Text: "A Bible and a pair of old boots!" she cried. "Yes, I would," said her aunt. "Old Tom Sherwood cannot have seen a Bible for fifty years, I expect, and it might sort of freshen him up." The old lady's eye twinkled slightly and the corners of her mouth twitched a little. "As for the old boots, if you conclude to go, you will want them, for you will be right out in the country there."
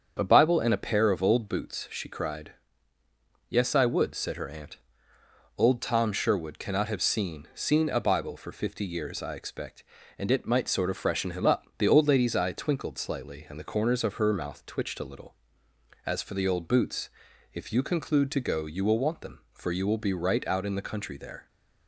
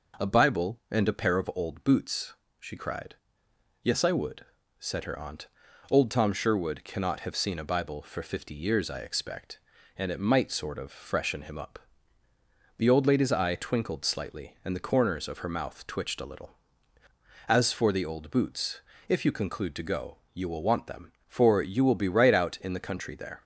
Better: second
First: starts louder than the rest; strong; until 1.2 s; 7 dB // says "seen" twice; at 7.5 s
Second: none

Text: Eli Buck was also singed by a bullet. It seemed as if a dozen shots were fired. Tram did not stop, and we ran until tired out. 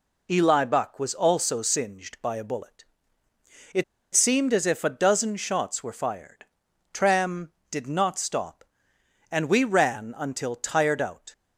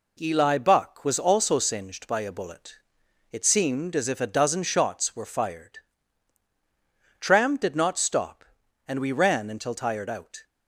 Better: second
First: pauses between "It" and "seemed"; slight; at 3.8 s; 0.30 s long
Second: none

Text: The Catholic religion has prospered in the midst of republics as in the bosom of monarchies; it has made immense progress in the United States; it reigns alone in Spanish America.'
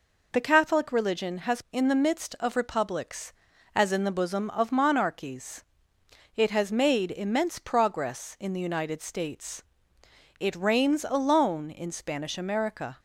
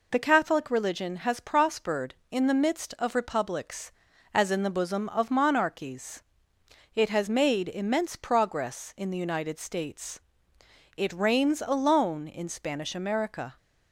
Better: second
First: skips "prospered"; at 1.6 s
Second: none

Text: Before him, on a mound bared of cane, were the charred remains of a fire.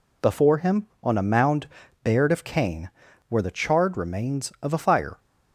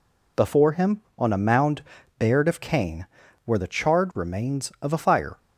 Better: neither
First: pauses between "mound" and "bared"; slight; at 1.6 s; 0.36 s long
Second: pauses between "mound" and "bared"; slight; at 1.8 s; 0.36 s long

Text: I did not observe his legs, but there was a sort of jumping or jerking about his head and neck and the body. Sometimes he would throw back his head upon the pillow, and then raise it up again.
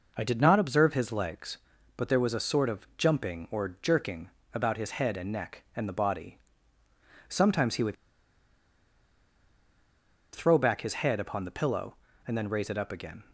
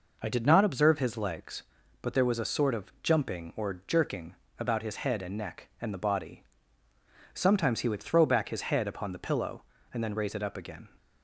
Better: second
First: pauses between "jerking" and "about"; slight; at 4.2 s; 0.24 s long // pauses between "would" and "throw"; strong; at 7.9 s; 2.3 s long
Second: pauses between "jerking" and "about"; slight; at 4.3 s; 0.24 s long

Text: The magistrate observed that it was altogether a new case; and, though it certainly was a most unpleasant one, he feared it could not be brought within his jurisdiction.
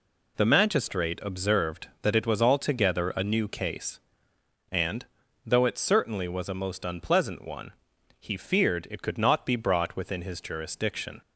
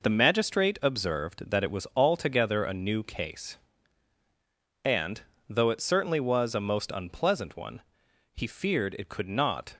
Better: first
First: none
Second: stops before "be brought within his jurisdiction"; at 9.7 s

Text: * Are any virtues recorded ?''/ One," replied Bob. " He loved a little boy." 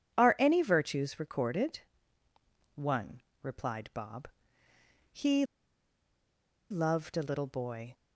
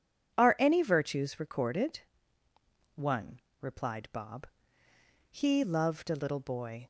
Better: second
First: starts louder than the rest; strong; until 1.1 s; 10 dB // pauses between "He" and "loved"; strong; at 5.4 s; 1.2 s long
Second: starts louder than the rest; strong; until 1.3 s; 10 dB

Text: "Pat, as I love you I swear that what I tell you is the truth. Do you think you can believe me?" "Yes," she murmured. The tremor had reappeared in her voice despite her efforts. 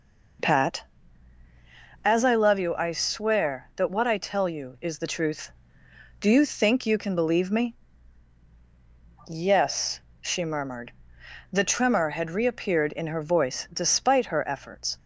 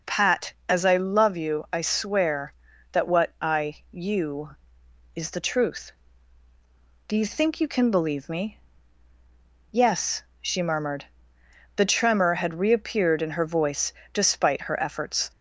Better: first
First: none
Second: skips "tell"; at 3.8 s // pauses between "voice" and "despite"; slight; at 13.9 s; 0.20 s long

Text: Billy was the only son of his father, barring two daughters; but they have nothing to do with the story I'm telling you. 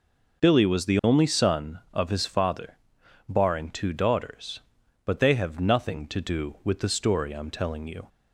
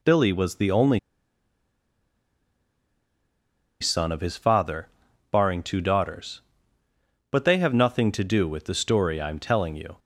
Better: first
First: none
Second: pauses between "only" and "son"; strong; at 0.9 s; 2.8 s long

